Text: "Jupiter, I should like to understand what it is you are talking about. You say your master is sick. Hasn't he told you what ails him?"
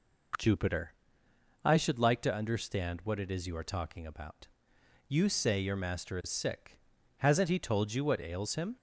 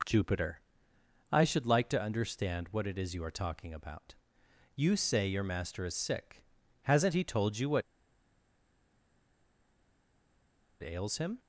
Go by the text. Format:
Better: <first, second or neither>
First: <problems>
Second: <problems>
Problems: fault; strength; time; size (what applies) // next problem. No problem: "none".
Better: first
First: none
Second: pauses between "what" and "ails"; strong; at 7.8 s; 3.0 s long